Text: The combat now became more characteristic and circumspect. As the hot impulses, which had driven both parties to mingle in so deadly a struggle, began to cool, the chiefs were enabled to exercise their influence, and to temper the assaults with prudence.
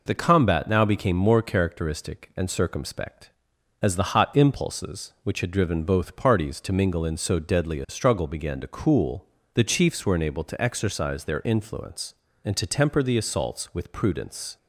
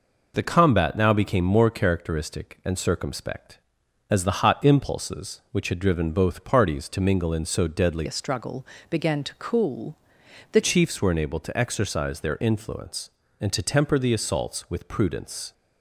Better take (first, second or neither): first